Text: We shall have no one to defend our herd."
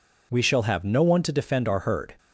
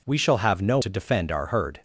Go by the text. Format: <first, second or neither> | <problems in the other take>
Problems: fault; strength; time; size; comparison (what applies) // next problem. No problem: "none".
first | skips "one"; at 0.7 s